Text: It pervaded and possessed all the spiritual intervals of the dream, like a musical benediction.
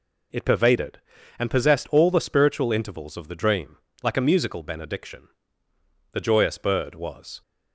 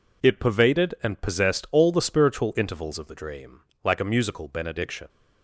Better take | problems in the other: second | goes on to say "The joyous bird was"; noticeable; from 6.1 s on; 1.2 s long

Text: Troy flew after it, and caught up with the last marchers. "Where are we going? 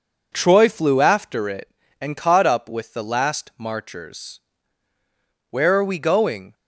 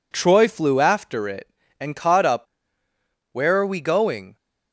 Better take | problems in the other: first | skips "with the last marchers"; at 2.8 s

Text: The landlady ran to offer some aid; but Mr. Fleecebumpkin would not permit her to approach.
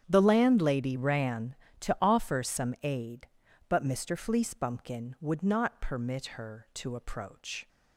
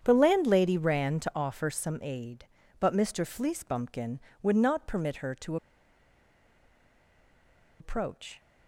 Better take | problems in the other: first | starts louder than the rest; strong; until 1.0 s; 8.5 dB; strong in the first // pauses between "to" and "approach"; strong; at 5.5 s; 2.2 s long

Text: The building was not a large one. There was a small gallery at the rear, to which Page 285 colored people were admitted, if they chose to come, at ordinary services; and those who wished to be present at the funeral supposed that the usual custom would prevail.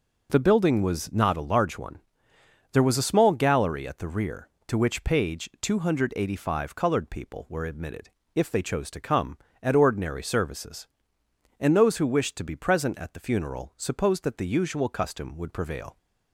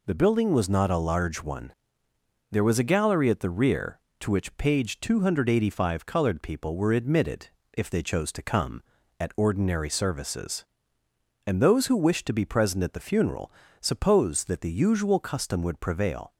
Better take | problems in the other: first | skips "small"; at 2.8 s // pauses between "funeral" and "supposed"; slight; at 13.5 s; 0.30 s long

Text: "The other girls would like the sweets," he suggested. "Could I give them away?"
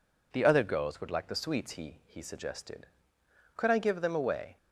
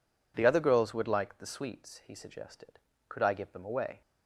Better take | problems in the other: second | says "he" twice; at 2.0 s

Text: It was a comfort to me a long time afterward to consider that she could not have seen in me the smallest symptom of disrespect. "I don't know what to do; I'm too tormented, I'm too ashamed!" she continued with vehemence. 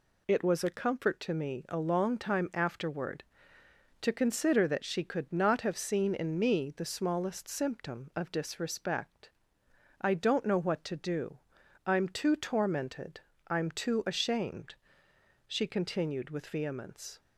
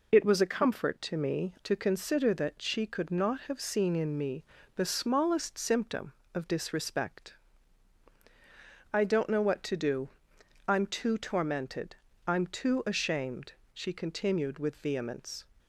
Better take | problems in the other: first | skips "a long time afterward"; at 1.5 s // pauses between "me" and "the"; slight; at 4.4 s; 0.30 s long

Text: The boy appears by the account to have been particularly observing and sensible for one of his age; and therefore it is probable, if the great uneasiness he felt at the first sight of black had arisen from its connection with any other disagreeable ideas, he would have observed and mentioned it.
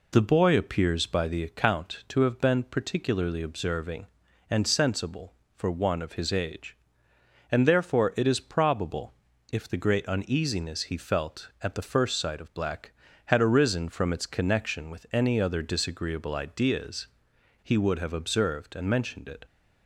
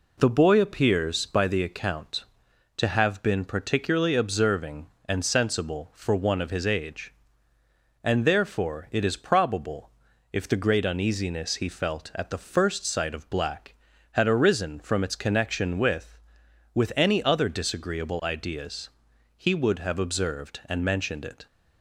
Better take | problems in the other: first | says "with" twice; at 16.7 s

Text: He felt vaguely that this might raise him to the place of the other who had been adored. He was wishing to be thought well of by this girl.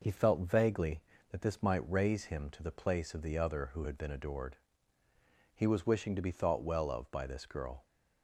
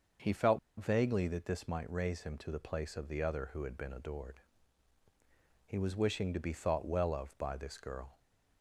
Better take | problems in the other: first | starts louder than the rest; until 1.4 s; 6 dB // pauses between "felt" and "vaguely"; slight; at 0.5 s; 0.19 s long

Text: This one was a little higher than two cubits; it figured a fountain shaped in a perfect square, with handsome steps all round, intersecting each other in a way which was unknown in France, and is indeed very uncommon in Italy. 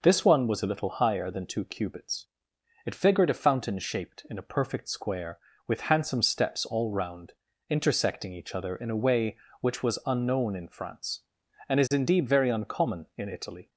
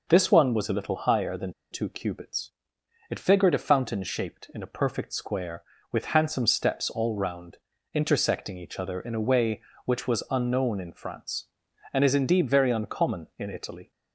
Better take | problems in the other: first | pauses between "than" and "two"; slight; at 1.5 s; 0.20 s long

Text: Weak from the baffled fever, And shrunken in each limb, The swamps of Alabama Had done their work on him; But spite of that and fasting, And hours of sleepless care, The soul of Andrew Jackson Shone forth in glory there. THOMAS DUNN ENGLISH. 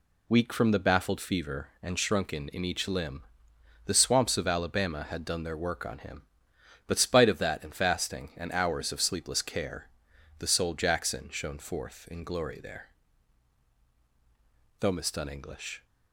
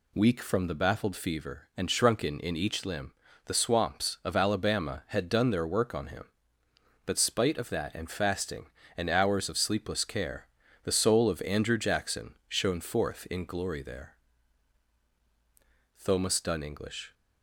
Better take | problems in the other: second | skips "of Andrew"; at 10.7 s

